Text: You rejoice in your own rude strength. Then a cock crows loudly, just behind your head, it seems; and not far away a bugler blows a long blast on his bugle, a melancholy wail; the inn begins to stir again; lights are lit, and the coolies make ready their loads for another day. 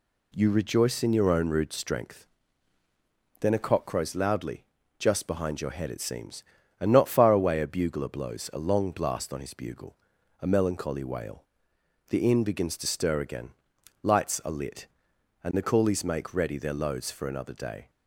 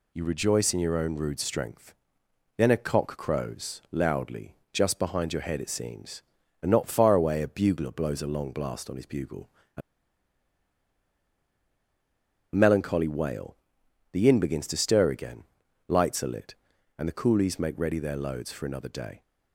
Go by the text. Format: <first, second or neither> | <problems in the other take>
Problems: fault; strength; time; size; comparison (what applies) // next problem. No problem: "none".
first | pauses between "a" and "melancholy"; strong; at 9.8 s; 2.7 s long